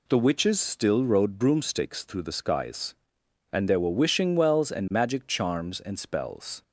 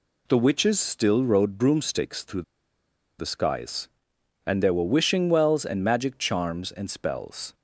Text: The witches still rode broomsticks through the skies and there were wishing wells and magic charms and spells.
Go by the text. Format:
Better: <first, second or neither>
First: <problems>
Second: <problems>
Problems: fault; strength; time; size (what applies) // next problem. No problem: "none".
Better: first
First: none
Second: pauses between "through" and "the"; noticeable; at 2.4 s; 0.77 s long